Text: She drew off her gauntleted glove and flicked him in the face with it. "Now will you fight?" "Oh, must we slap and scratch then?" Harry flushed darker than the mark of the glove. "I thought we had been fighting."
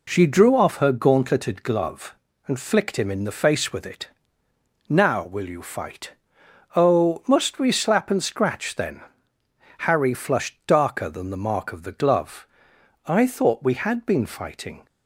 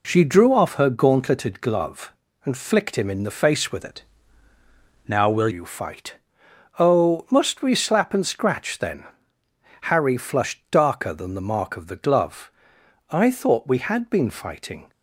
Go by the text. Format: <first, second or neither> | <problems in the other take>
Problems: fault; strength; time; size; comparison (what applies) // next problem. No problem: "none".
first | changes voice from "it" to "will"; from 3.8 to 5.4 s; 1.6 s long